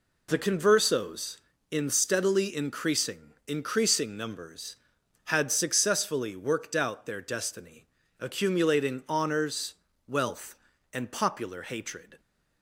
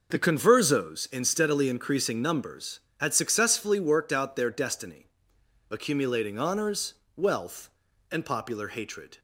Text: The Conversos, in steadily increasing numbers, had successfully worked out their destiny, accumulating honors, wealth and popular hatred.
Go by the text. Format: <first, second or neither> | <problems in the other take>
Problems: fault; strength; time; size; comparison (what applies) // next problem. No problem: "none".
second | says "increasing" twice; at 3.4 s